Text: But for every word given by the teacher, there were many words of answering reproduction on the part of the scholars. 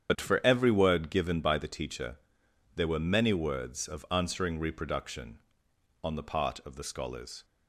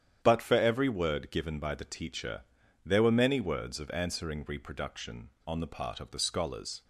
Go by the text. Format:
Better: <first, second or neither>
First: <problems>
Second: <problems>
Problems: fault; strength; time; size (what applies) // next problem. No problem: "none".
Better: second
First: loses the start of "But"; at 0.0 s; 40 ms // starts louder than the rest; strong; until 1.1 s; 8.5 dB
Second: starts louder than the rest; strong; until 1.2 s; 9.5 dB